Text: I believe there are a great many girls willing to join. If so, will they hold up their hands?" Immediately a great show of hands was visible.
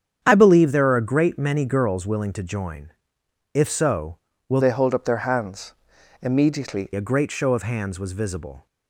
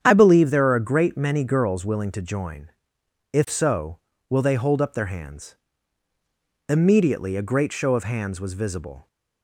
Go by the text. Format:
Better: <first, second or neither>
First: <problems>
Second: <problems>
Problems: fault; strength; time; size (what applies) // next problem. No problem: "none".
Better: second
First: starts louder than the rest; strong; until 1.2 s; 8 dB // changes voice from "they" to "Immediately"; from 4.6 to 6.9 s; 2.3 s long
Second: starts louder than the rest; strong; until 1.0 s; 9 dB